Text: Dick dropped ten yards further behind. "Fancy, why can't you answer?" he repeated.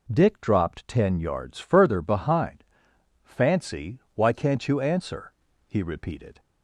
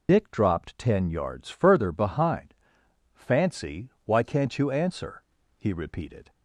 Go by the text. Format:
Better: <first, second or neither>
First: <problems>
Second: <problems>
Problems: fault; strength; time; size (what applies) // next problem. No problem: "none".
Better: first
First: none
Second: loses the start of "Dick"; at 0.0 s; 115 ms